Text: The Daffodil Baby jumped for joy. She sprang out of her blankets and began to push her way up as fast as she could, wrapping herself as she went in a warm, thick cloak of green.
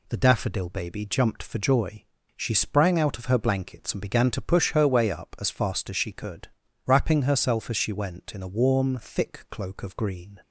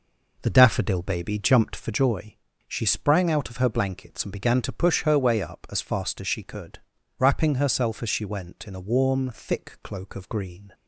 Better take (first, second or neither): first